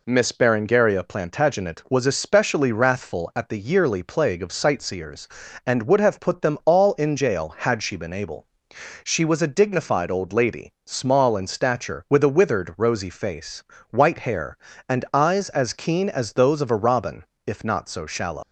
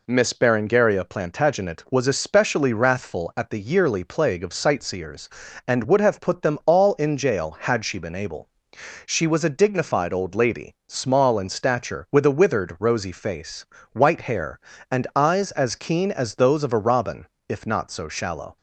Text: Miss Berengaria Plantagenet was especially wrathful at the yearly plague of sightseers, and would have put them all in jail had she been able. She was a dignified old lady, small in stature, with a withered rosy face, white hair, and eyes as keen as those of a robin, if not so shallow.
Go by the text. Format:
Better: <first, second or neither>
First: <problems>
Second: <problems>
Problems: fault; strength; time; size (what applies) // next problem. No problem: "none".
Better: second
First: leaves "shallow" unfinished; at 18.4 s; 115 ms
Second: none